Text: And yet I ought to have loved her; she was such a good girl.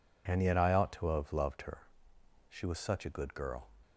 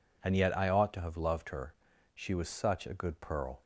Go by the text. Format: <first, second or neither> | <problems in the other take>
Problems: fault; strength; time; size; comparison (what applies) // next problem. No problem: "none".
first | says "pearl" for "girl"; at 3.2 s